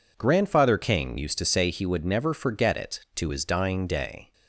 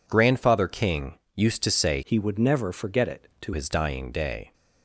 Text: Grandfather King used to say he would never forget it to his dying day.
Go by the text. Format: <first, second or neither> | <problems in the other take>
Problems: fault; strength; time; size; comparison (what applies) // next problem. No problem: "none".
first | pauses between "King" and "used"; slight; at 1.1 s; 0.16 s long // changes voice from "he" to "to"; from 2.0 to 3.5 s; 1.5 s long